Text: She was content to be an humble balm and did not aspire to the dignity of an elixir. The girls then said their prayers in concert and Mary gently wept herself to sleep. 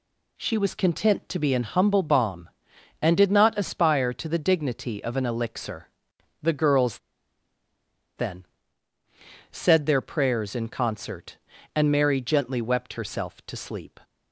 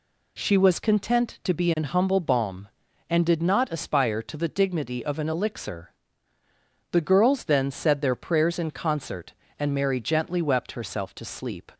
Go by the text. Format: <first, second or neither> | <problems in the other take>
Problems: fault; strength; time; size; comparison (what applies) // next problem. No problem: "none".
second | pauses between "girls" and "then"; at 6.9 s; 1.1 s long // pauses between "then" and "said"; at 8.4 s; 1.0 s long